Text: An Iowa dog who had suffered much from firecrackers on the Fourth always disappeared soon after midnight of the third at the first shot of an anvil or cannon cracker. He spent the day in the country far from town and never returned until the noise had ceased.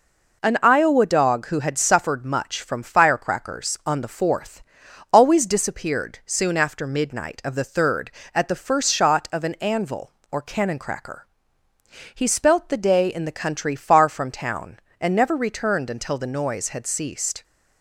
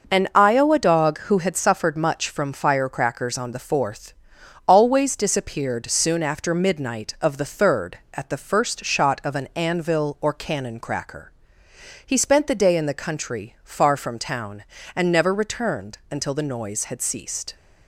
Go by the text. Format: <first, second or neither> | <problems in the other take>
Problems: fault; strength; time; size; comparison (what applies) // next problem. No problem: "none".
second | pauses between "Fourth" and "always"; noticeable; at 4.6 s; 0.50 s long; noticeable in the second // says "spelt" for "spent"; at 12.2 s